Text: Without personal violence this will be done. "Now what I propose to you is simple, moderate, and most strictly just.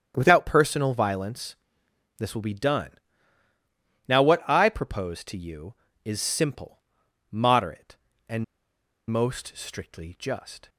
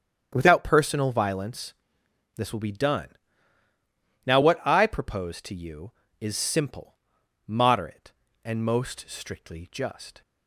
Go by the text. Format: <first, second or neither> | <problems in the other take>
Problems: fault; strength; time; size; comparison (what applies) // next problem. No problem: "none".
second | starts louder than the rest; strong; until 1.1 s; 8.5 dB; strong in the second // pauses between "violence" and "this"; noticeable; at 1.5 s; 0.62 s long; noticeable in the second // pauses between "and" and "most"; noticeable; at 8.4 s; 0.66 s long